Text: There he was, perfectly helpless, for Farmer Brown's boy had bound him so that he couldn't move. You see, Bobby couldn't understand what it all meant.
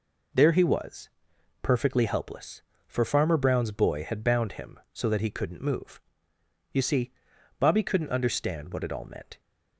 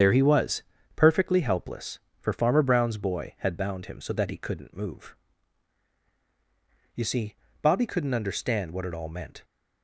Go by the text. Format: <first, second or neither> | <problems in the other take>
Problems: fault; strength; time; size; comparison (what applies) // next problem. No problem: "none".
first | loses the start of "There"; at 0.0 s; 65 ms // starts louder than the rest; strong; until 1.3 s; 8 dB